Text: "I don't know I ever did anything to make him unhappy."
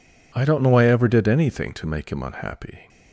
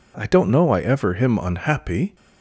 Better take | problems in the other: first | skips "did anything to make"; at 1.1 s

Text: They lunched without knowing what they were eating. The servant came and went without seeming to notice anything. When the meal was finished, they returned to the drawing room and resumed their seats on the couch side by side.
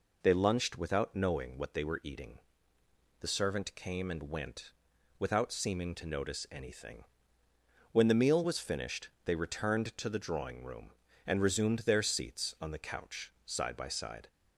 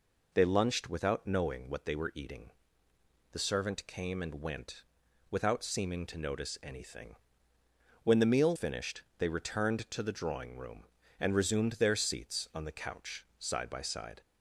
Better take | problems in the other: first | pauses between "went" and "without"; noticeable; at 4.8 s; 0.46 s long; noticeable in the first // skips "was"; at 8.5 s

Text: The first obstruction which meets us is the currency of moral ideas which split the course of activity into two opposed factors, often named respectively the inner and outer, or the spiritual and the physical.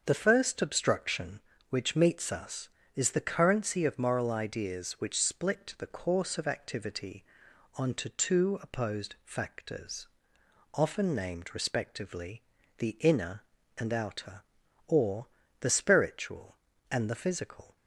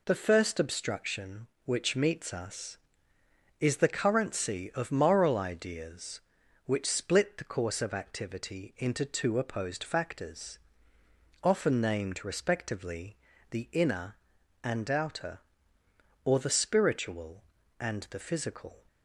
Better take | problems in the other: second | starts louder than the rest; until 1.0 s; 6.5 dB // says "onto" for "into"; at 7.7 s // pauses between "respectively" and "the"; at 12.4 s; 0.38 s long; slight in the second // pauses between "or" and "the"; slight; at 15.2 s; 0.32 s long

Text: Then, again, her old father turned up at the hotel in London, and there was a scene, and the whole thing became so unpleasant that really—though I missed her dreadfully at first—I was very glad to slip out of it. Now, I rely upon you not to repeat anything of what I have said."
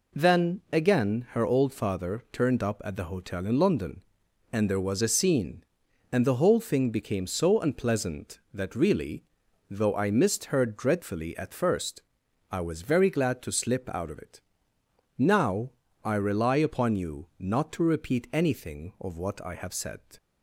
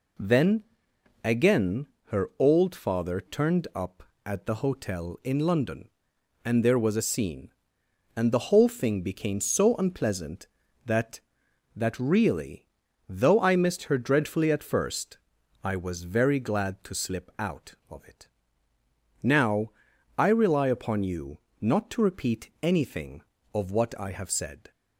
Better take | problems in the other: first | says "that" twice; at 11.7 s // pauses between "you" and "not"; slight; at 21.3 s; 0.22 s long

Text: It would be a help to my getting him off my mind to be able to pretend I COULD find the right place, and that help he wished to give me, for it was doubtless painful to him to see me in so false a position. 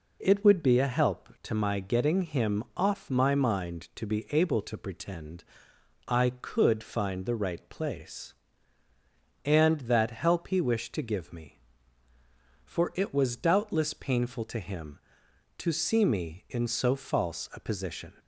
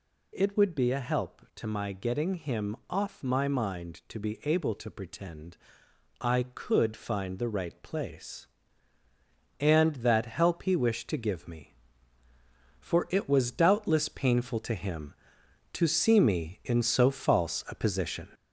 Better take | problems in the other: first | gets louder; throughout; 4 dB // pauses between "pretend" and "I"; noticeable; at 5.5 s; 0.64 s long; noticeable in the first

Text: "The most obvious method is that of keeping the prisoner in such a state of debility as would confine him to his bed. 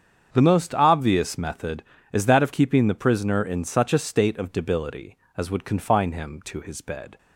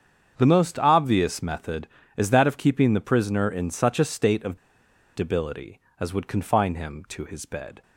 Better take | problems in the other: first | starts louder than the rest; strong; until 1.3 s; 7.5 dB; strong in the first // pauses between "of" and "debility"; noticeable; at 4.5 s; 0.57 s long

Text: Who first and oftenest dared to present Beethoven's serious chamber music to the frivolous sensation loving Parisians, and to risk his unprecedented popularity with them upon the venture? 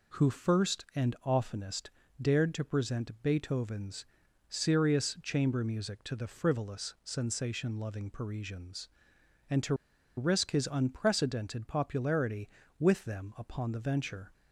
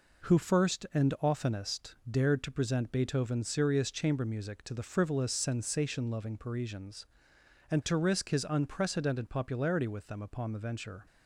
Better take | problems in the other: second | pauses between "oftenest" and "dared"; slight; at 1.8 s; 0.32 s long // pauses between "Beethoven's" and "serious"; noticeable; at 4.0 s; 0.46 s long // pauses between "to" and "risk"; at 9.7 s; 0.43 s long

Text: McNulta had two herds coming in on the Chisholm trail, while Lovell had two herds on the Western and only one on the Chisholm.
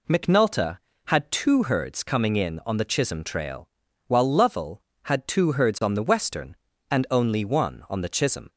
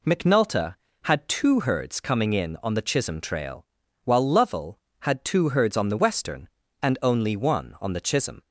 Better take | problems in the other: neither | none

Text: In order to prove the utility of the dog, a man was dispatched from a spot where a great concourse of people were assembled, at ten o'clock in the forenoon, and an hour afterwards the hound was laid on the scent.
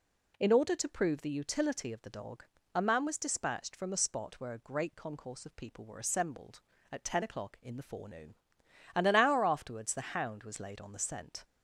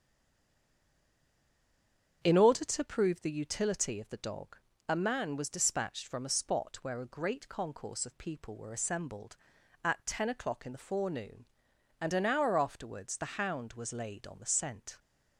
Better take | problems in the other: first | stays silent before the first word; until 2.2 s; 2.2 s long // starts louder than the rest; strong; until 3.2 s; 7.5 dB

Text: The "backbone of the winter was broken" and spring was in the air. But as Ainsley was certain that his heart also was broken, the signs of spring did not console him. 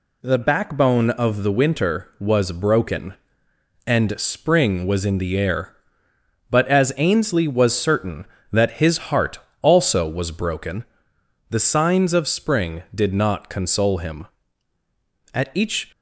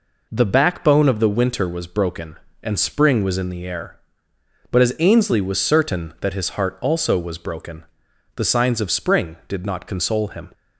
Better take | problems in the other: second | pauses between "heart" and "also"; slight; at 9.3 s; 0.24 s long // goes on to say "At each"; from 15.3 s on; 0.58 s long

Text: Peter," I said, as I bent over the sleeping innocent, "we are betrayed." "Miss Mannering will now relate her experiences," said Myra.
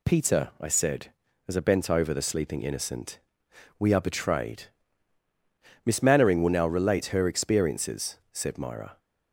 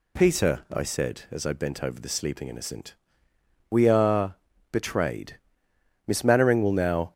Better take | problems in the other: first | pauses between "are" and "betrayed"; slight; at 4.3 s; 0.34 s long // stops before "relate her experiences said Myra"; at 7.1 s

